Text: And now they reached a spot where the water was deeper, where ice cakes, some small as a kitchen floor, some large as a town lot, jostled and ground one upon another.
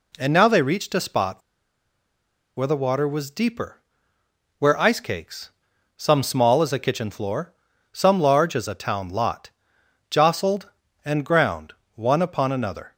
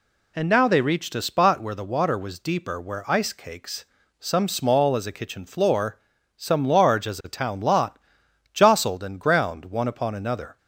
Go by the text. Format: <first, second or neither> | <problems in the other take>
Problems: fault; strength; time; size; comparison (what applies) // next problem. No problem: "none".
second | pauses between "spot" and "where"; at 1.4 s; 1.1 s long // pauses between "ground" and "one"; slight; at 11.7 s; 0.22 s long